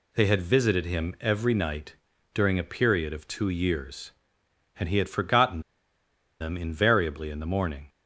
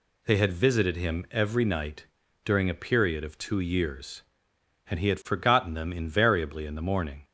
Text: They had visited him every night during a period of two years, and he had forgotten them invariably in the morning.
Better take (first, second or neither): second